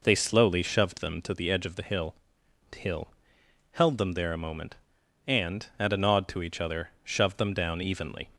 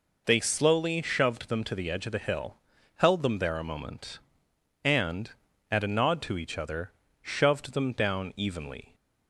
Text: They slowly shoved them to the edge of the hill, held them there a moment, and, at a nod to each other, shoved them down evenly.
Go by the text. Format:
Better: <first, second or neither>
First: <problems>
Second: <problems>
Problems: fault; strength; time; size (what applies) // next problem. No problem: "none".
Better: second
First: says "hill" twice; at 2.7 s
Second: none